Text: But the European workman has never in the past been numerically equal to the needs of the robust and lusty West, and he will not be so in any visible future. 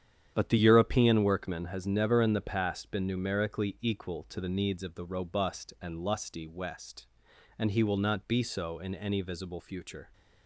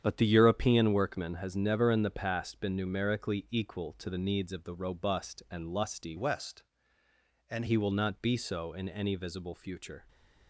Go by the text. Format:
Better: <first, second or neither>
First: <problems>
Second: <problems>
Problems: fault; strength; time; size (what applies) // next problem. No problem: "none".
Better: first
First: starts louder than the rest; strong; until 1.3 s; 9 dB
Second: starts louder than the rest; strong; until 1.0 s; 8.5 dB // changes voice from "West" to "and"; from 6.1 to 7.6 s; 1.5 s long